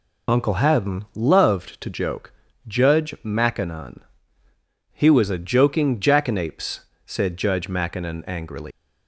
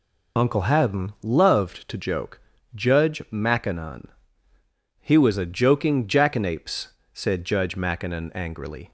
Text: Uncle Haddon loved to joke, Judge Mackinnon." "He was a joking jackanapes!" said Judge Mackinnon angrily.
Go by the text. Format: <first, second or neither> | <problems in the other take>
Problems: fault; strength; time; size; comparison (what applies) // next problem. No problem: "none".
second | leaves "angrily" unfinished; at 8.7 s; 125 ms